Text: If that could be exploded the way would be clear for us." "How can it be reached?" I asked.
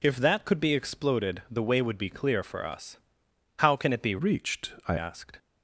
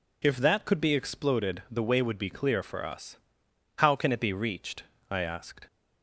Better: second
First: changes voice from "reached" to "I"; from 4.1 to 4.9 s; 0.8 s long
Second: none

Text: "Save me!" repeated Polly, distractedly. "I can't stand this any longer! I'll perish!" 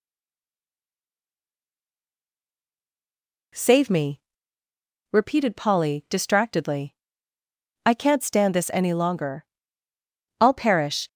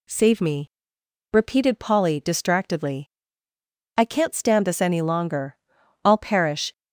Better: second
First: stays silent before the first word; strong; until 3.5 s; 3.5 s long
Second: none

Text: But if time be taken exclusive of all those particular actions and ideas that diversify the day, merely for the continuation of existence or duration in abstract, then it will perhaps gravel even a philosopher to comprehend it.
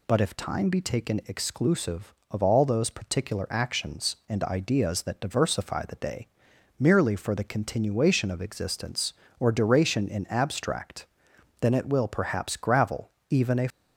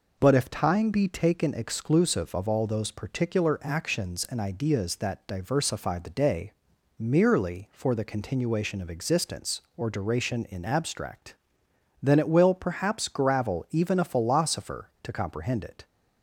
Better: second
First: pauses between "gravel" and "even"; slight; at 13.1 s; 0.18 s long // stops before "philosopher to comprehend it"; at 13.7 s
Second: none

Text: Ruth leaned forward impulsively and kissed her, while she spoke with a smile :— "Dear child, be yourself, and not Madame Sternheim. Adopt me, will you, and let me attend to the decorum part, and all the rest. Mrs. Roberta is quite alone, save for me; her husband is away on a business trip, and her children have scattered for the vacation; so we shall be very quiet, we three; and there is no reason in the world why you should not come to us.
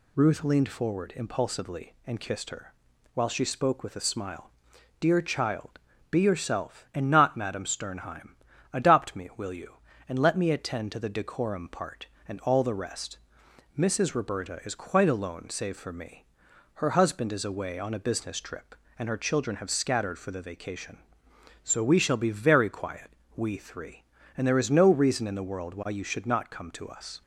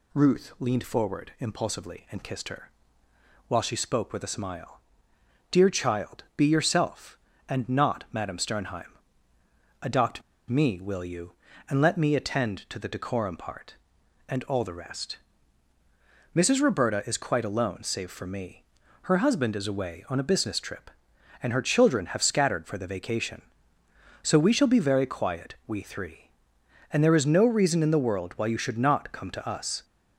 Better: first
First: none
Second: pauses between "Adopt" and "me"; slight; at 10.2 s; 0.28 s long

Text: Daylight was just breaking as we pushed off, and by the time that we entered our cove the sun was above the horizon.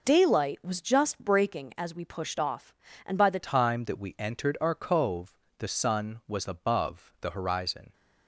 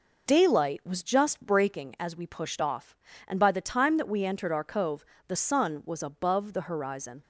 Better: second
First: changes voice at "time"; from 3.4 s on; 4.5 s long // pauses between "cove" and "the"; slight; at 5.3 s; 0.24 s long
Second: pauses between "cove" and "the"; slight; at 5.0 s; 0.24 s long

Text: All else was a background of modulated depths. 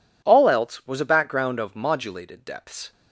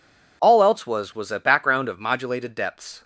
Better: first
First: none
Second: says "was" twice; at 1.1 s

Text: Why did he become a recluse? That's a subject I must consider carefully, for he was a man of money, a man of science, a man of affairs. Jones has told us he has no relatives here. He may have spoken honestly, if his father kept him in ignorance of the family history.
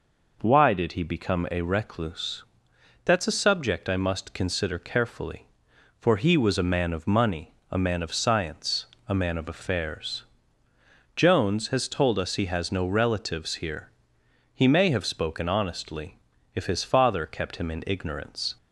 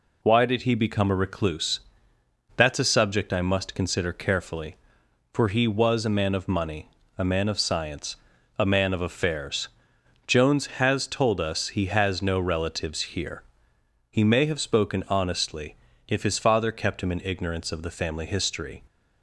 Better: second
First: stops before "of the family history"; at 18.5 s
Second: none

